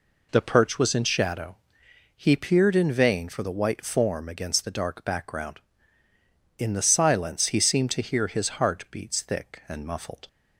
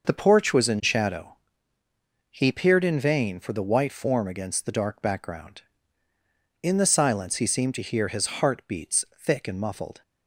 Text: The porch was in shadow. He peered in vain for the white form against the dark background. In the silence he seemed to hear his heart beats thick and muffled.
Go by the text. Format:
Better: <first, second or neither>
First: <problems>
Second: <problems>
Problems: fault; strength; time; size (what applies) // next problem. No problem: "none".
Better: second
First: says "perch" for "porch"; at 0.4 s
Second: none